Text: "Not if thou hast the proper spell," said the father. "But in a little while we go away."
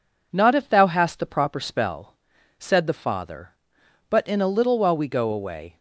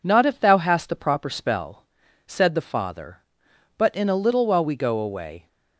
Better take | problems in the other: neither | none

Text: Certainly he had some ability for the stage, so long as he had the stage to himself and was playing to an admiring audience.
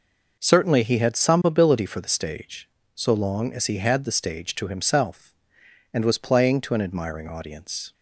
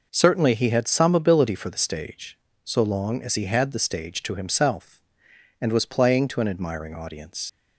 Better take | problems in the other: first | leaves "audience" unfinished; at 7.4 s; 95 ms

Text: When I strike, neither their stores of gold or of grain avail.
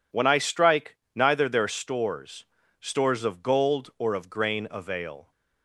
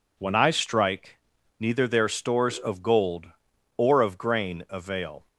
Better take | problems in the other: second | says "stores" twice; at 2.8 s

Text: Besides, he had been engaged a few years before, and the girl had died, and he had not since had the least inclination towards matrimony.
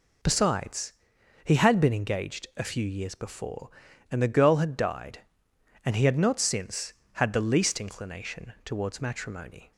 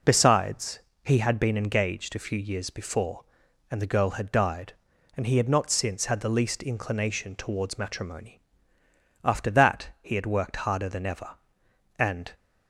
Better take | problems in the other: first | goes on to say "After that he had worked harder than ever and"; strong; from 9.2 s on; 3.1 s long

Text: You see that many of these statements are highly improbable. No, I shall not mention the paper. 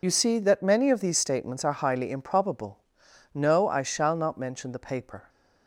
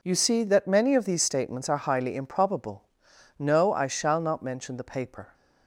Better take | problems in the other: second | loses the start of "You"; at 0.0 s; 45 ms

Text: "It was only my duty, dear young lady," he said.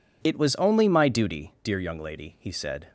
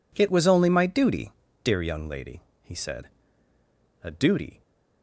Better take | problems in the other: first | goes on to say "A duty"; from 4.0 s on; 0.58 s long

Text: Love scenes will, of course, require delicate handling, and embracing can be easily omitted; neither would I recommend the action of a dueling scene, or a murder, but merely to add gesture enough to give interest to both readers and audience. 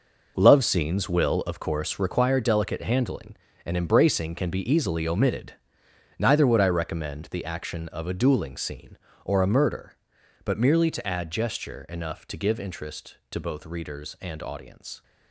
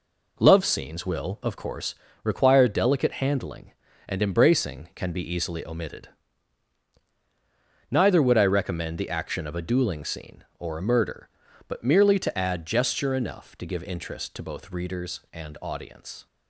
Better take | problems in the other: second | gets quieter; strong; throughout; 11 dB

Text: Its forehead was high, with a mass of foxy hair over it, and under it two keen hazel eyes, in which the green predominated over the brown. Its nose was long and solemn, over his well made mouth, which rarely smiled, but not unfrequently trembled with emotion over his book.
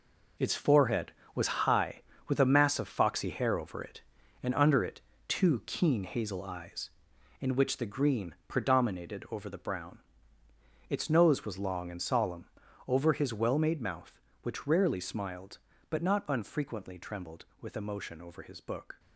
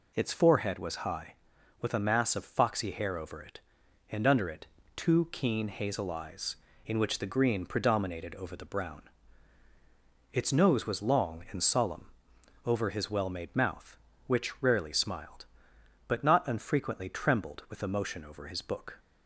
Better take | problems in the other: second | gets quieter; strong; throughout; 9.5 dB // pauses between "it" and "two"; slight; at 5.0 s; 0.26 s long; slight in the second

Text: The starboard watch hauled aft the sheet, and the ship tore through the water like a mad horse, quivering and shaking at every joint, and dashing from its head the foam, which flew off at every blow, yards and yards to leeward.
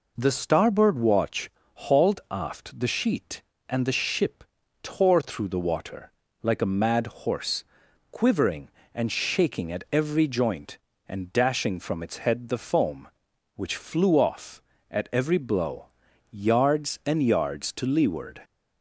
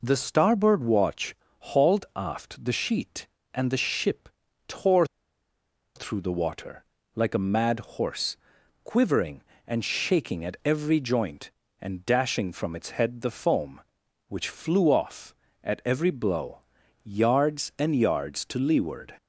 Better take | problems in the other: first | pauses between "watch" and "hauled"; slight; at 1.3 s; 0.24 s long; slight in the first // pauses between "ship" and "tore"; slight; at 4.3 s; 0.36 s long; slight in the first // pauses between "tore" and "through"; noticeable; at 5.0 s; 0.91 s long // pauses between "water" and "like"; slight; at 6.8 s; 0.32 s long; slight in the first

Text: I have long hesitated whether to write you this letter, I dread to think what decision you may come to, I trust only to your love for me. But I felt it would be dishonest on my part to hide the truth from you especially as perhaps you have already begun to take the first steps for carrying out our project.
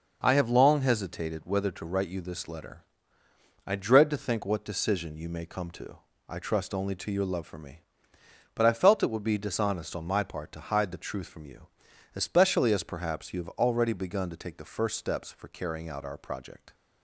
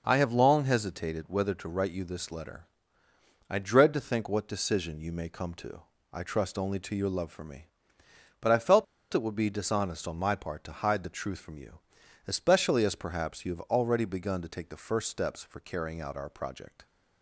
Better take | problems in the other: first | pauses between "felt" and "it"; slight; at 8.8 s; 0.28 s long // pauses between "you" and "especially"; noticeable; at 11.7 s; 0.48 s long; noticeable in the first

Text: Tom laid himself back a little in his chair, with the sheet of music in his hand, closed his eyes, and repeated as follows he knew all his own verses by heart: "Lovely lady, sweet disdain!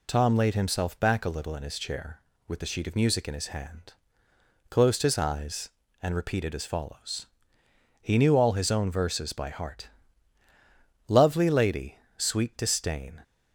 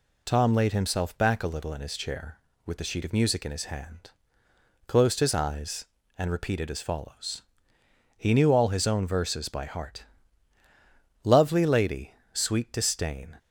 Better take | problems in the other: neither | pauses between "follows" and "he"; noticeable; the same in both

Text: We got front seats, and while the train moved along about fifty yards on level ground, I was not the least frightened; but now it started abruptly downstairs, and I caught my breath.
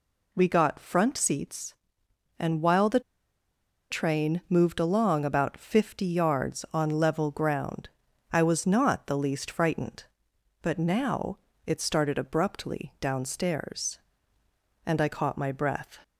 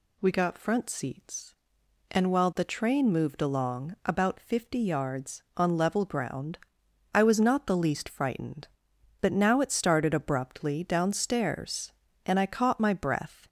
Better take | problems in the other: second | pauses between "the" and "train"; noticeable; at 2.9 s; 0.90 s long // pauses between "now" and "it"; slight; at 11.3 s; 0.28 s long

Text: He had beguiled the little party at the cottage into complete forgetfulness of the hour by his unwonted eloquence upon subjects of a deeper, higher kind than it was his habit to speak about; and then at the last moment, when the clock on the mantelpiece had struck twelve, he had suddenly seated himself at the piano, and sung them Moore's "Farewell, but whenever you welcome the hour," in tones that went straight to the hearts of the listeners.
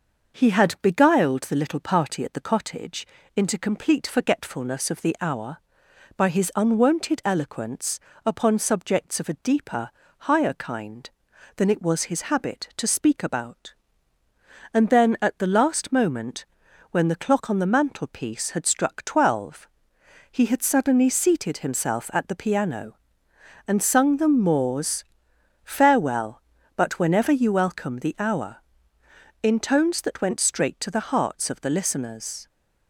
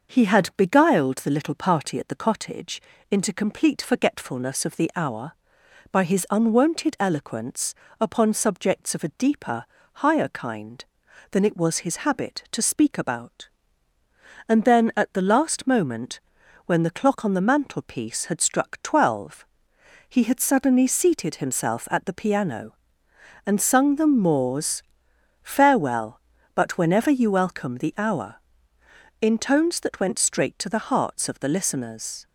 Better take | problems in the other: neither | starts louder than the rest; noticeable; the same in both // pauses between "cottage" and "into"; slight; the same in both // pauses between "eloquence" and "upon"; slight; the same in both // pauses between "Moore's" and "Farewell"; noticeable; the same in both

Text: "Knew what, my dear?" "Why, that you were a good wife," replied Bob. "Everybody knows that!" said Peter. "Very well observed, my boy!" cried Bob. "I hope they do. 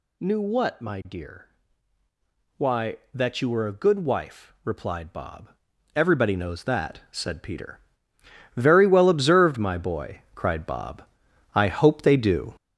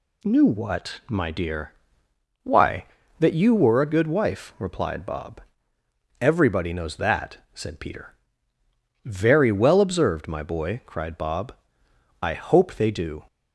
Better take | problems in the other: second | gets louder; noticeable; throughout; 5 dB

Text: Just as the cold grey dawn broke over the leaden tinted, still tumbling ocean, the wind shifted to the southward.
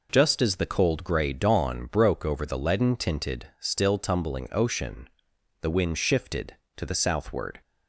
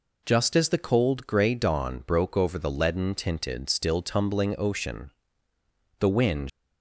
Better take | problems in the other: first | stops before "shifted to the southward"; at 6.4 s

